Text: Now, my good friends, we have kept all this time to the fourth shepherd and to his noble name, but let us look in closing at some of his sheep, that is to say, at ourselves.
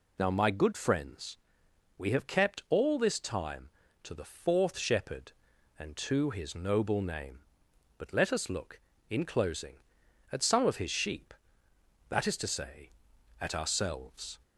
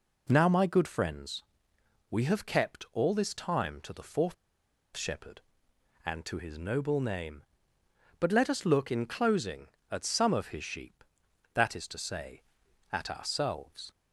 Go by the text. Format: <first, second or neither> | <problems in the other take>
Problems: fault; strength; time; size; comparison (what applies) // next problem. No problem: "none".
first | pauses between "fourth" and "shepherd"; noticeable; at 4.3 s; 0.61 s long